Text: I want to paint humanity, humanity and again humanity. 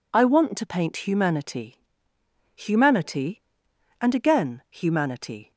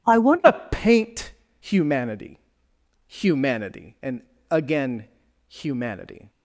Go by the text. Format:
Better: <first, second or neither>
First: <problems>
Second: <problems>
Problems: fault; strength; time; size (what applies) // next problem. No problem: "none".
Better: first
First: none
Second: changes voice at "to"; from 0.4 s on; 5.8 s long // pauses between "to" and "paint"; slight; at 0.5 s; 0.18 s long // pauses between "paint" and "humanity"; slight; at 1.3 s; 0.28 s long // pauses between "and" and "again"; slight; at 4.2 s; 0.28 s long // pauses between "again" and "humanity"; at 5.0 s; 0.42 s long